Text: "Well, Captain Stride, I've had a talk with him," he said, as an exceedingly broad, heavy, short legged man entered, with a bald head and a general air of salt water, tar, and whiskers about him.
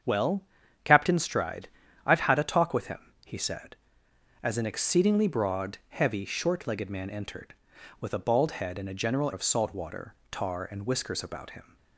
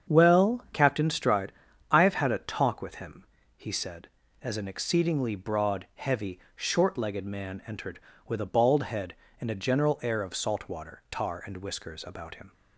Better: second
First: starts louder than the rest; strong; until 1.4 s; 7.5 dB // skips "air"; at 9.3 s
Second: starts louder than the rest; strong; until 1.1 s; 7.5 dB

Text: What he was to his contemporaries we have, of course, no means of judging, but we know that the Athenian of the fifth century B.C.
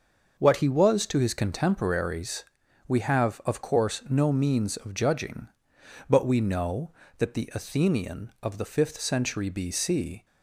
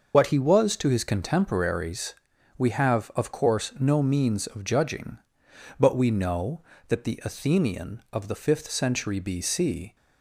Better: first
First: starts louder than the rest; until 1.3 s; 6 dB // pauses between "contemporaries" and "we"; at 2.4 s; 0.42 s long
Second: loses the start of "What"; at 0.1 s; 55 ms // starts louder than the rest; noticeable; until 1.1 s; 6 dB // pauses between "contemporaries" and "we"; at 2.1 s; 0.42 s long

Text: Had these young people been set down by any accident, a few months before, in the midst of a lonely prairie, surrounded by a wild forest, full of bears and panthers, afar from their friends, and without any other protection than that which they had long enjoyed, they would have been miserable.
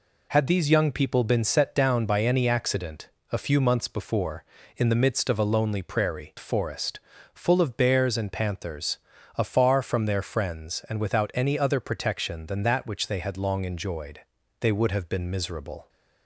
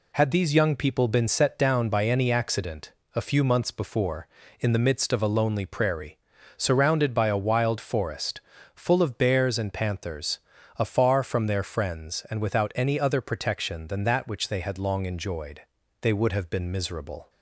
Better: second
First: skips "surrounded by a wild"; at 6.3 s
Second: none

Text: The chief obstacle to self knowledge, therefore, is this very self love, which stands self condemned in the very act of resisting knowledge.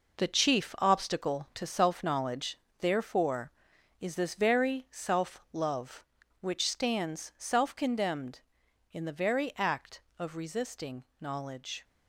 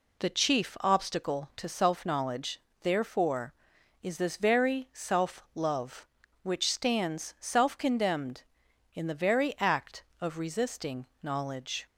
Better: second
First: gets quieter; strong; throughout; 8 dB // pauses between "resisting" and "knowledge"; slight; at 11.0 s; 0.16 s long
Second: pauses between "resisting" and "knowledge"; slight; at 11.0 s; 0.16 s long

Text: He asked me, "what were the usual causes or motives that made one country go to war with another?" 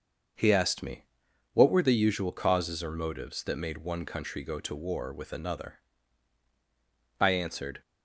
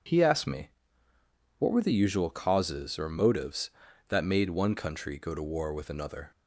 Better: second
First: starts louder than the rest; until 1.8 s; 6.5 dB // goes on to say "I answered"; from 7.2 s on; 0.60 s long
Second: none

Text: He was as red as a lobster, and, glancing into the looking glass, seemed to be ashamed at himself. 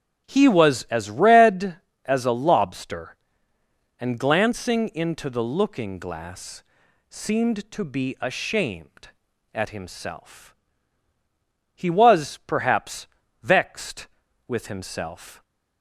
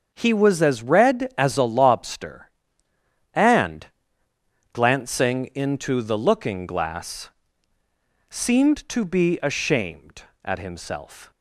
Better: second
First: starts louder than the rest; strong; until 1.2 s; 8.5 dB // goes on to say "He was perhaps vexed with himself"; strong; from 11.7 s on; 3.6 s long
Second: starts louder than the rest; until 1.1 s; 6.5 dB

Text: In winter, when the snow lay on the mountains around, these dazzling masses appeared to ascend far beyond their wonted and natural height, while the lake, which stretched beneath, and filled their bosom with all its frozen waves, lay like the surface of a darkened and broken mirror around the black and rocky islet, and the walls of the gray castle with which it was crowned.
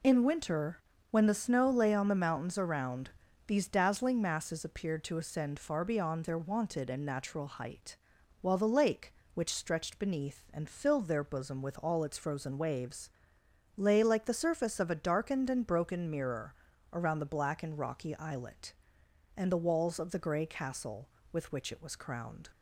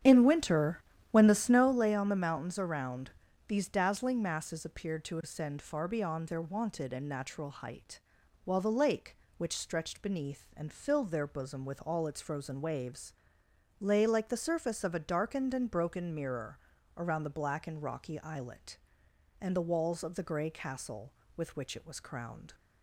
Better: first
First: pauses between "mirror" and "around"; at 16.5 s; 0.40 s long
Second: starts louder than the rest; strong; until 1.8 s; 9 dB // pauses between "mirror" and "around"; at 16.5 s; 0.40 s long

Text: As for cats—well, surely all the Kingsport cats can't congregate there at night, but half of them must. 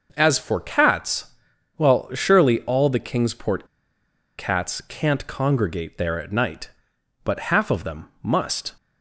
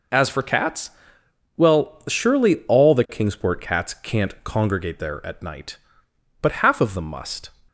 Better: second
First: pauses between "Kingsport" and "cats"; noticeable; at 3.6 s; 0.73 s long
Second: none

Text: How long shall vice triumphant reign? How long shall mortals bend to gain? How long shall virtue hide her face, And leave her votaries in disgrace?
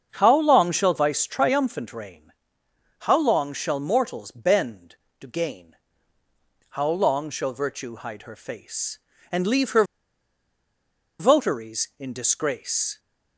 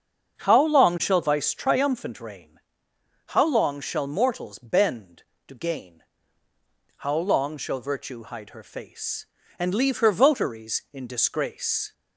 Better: second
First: starts louder than the rest; until 1.1 s; 7 dB // pauses between "her" and "votaries"; strong; at 9.8 s; 1.3 s long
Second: starts louder than the rest; until 1.4 s; 7 dB

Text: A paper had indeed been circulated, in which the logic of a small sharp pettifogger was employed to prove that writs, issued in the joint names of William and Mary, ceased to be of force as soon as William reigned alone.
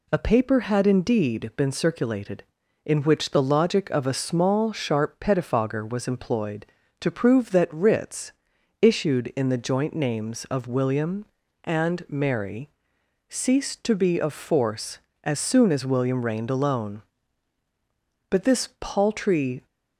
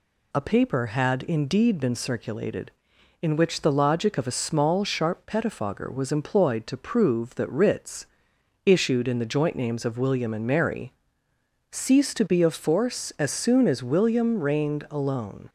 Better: second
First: goes on to say "But this paltry"; from 18.2 s on; 1.3 s long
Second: none

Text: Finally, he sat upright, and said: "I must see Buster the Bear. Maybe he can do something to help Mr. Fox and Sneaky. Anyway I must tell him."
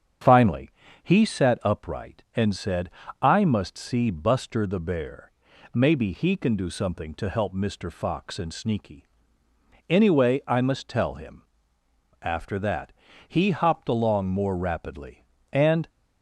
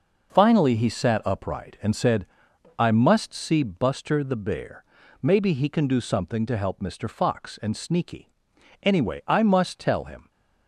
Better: second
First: starts louder than the rest; strong; until 1.5 s; 8 dB // goes on to say "After that he hopped along more rapidly and"; strong; from 12.2 s on; 3.6 s long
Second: none

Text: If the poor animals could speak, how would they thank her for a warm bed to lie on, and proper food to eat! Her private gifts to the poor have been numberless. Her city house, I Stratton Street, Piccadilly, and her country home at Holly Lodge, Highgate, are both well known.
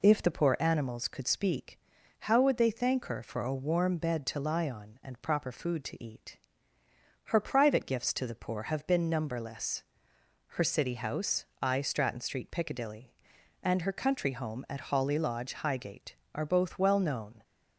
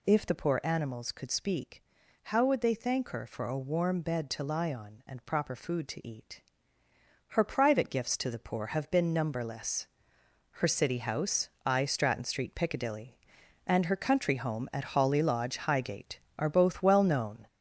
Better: first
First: none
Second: gets louder; noticeable; throughout; 5 dB

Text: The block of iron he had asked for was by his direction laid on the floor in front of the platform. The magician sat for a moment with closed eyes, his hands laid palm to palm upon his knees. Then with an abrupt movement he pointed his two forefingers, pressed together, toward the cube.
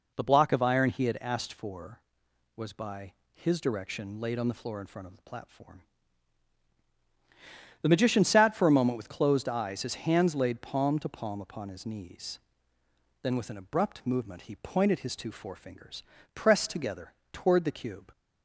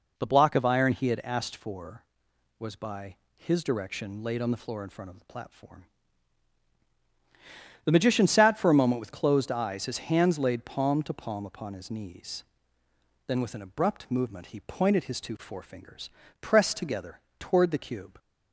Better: neither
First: pauses between "by" and "his"; slight; at 3.1 s; 0.20 s long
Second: pauses between "by" and "his"; slight; at 3.1 s; 0.20 s long

